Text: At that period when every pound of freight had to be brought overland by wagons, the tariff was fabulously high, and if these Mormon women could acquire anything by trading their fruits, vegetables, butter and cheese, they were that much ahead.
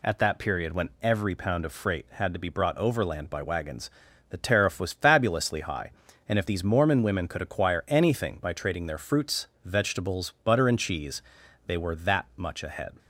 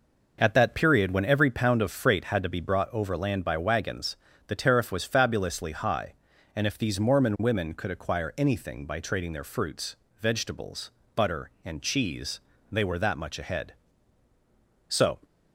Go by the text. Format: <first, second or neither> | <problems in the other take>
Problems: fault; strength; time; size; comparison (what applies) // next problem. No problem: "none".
first | goes on to say "So"; slight; from 14.8 s on; 0.34 s long